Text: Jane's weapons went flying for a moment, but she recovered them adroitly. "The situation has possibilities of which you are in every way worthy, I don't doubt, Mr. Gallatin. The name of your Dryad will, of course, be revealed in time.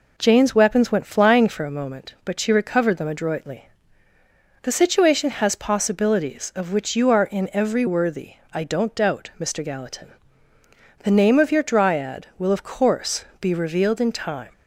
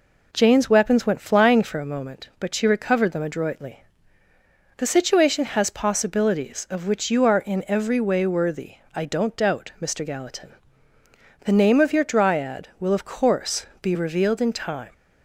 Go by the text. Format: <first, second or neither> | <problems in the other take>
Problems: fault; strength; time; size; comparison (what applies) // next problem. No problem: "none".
second | skips "way"; at 7.8 s